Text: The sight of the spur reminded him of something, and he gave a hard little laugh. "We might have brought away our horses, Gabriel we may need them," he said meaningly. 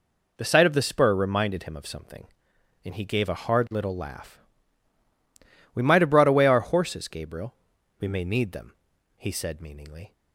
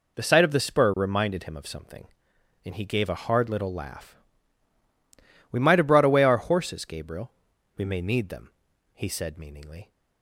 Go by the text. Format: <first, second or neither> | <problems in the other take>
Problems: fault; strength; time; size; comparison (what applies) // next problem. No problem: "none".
neither | pauses between "Gabriel" and "we"; the same in both